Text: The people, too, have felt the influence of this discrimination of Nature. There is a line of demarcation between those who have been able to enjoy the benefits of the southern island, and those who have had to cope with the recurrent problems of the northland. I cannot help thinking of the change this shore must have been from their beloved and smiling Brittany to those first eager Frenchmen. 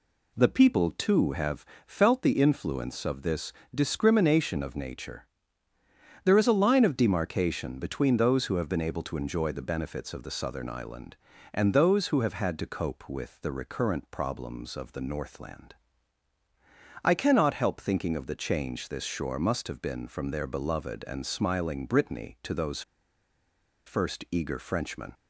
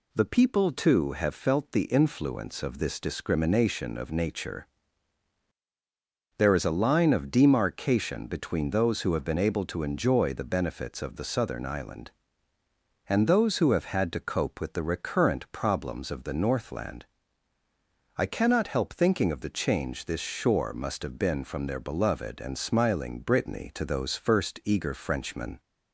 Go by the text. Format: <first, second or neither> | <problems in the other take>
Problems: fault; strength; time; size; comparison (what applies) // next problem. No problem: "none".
second | pauses between "have" and "felt"; slight; at 1.6 s; 0.22 s long // pauses between "this" and "discrimination"; slight; at 3.5 s; 0.20 s long // pauses between "those" and "first"; at 22.8 s; 1.0 s long